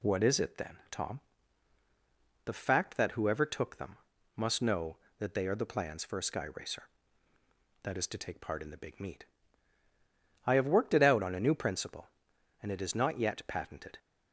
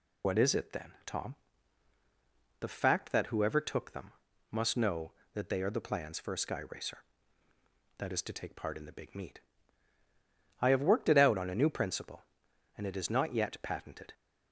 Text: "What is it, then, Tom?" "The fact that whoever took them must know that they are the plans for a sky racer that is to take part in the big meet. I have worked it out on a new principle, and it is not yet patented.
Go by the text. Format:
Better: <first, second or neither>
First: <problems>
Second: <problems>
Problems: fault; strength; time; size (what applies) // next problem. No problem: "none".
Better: first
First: pauses between "them" and "must"; slight; at 3.9 s; 0.36 s long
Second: loses the start of "What"; at 0.2 s; 75 ms // pauses between "them" and "must"; slight; at 4.1 s; 0.36 s long